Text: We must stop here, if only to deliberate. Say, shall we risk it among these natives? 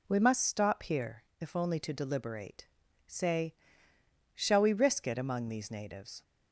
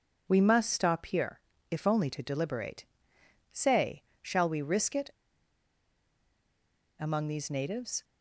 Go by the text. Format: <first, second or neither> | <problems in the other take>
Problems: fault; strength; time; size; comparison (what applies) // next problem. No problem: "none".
first | pauses between "it" and "among"; strong; at 5.0 s; 1.9 s long